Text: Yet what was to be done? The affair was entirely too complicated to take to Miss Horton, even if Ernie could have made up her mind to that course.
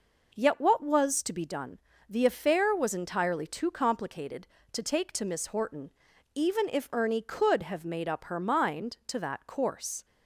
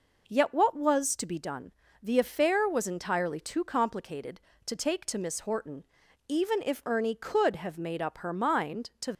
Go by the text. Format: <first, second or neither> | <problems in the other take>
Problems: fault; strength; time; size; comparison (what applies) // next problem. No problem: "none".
first | stops before "that course"; at 9.1 s